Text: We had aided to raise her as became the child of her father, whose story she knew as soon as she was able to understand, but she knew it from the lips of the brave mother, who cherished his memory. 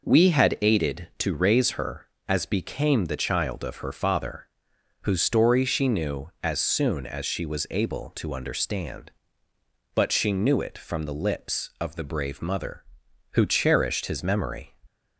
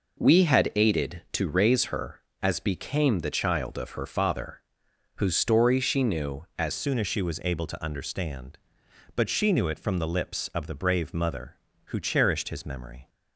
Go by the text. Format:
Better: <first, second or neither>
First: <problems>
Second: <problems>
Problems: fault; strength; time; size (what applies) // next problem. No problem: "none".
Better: first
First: none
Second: changes voice at "soon"; from 6.7 s on; 6.3 s long